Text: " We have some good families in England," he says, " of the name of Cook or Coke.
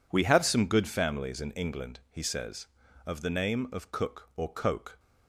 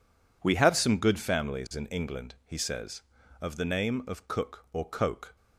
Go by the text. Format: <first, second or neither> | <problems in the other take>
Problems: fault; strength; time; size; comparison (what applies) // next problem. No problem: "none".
neither | none